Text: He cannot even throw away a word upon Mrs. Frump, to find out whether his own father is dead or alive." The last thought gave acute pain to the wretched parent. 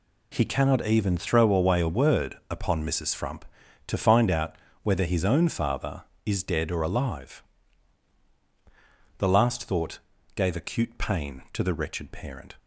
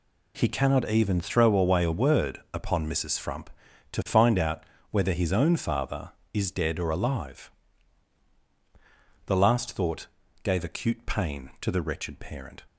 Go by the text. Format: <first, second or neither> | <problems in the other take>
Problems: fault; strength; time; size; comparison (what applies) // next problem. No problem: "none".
neither | pauses between "out" and "whether"; slight; the same in both // pauses between "thought" and "gave"; the same in both